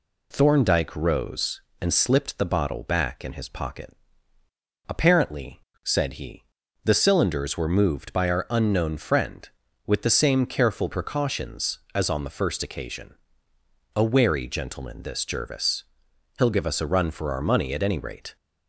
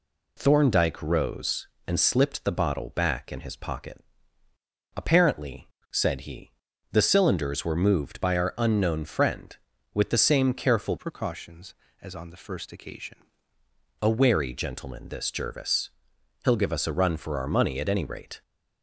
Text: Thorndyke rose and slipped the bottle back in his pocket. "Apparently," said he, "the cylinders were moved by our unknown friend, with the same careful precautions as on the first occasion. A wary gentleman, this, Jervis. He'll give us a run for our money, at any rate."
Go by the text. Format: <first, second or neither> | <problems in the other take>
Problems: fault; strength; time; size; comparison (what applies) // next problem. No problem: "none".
first | changes voice from "precautions" to "occasion"; from 10.9 to 13.1 s; 2.2 s long